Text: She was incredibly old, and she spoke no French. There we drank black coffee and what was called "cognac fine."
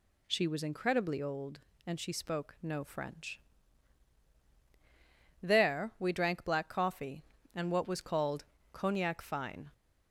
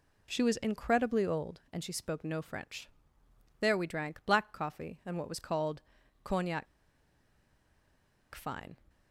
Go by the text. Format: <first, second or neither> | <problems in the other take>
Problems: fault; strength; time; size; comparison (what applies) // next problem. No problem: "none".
first | pauses between "called" and "cognac"; at 5.8 s; 0.42 s long; slight in the first // pauses between "cognac" and "fine"; strong; at 6.6 s; 1.6 s long